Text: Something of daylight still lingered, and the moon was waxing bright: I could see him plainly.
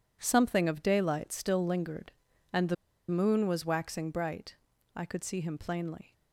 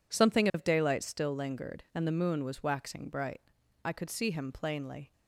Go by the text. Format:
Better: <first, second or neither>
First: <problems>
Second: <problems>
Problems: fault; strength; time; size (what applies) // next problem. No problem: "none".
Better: second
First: pauses between "the" and "moon"; slight; at 2.7 s; 0.33 s long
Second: none